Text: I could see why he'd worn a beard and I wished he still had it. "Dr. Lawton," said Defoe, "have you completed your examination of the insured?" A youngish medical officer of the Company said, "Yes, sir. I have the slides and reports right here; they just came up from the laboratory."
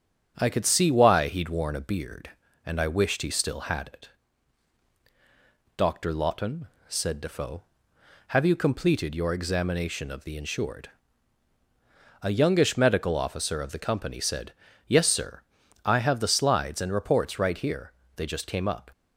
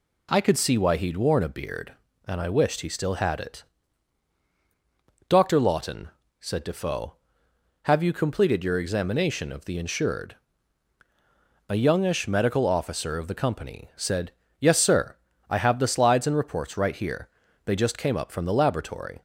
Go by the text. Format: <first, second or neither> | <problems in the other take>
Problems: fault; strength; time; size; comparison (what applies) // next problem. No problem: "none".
second | starts louder than the rest; strong; until 1.3 s; 8 dB // stops before "from the laboratory"; at 18.9 s